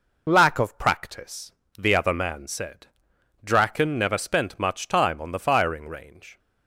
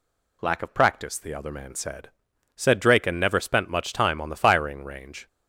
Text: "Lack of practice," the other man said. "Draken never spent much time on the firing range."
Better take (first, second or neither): first